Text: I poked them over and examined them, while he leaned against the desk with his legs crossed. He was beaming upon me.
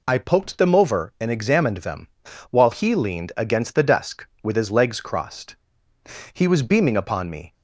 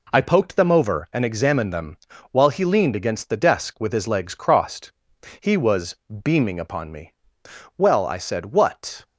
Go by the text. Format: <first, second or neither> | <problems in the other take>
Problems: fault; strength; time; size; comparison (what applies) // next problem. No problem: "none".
first | pauses between "was" and "beaming"; slight; at 5.9 s; 0.28 s long // goes on to say "Well I said what"; noticeable; from 7.7 s on; 1.2 s long